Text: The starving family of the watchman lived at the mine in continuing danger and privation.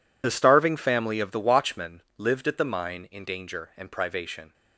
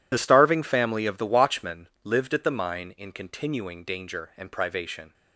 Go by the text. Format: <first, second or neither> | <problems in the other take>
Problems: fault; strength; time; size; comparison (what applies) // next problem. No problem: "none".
second | pauses between "watchman" and "lived"; slight; at 2.0 s; 0.16 s long; slight in the second // skips "continuing"; at 3.2 s